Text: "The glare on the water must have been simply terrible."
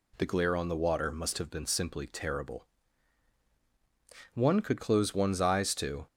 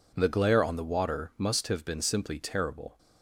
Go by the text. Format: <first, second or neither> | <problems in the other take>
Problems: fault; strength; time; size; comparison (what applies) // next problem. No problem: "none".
second | goes on to say "One could close one's eyes to"; strong; from 4.3 s on; 1.7 s long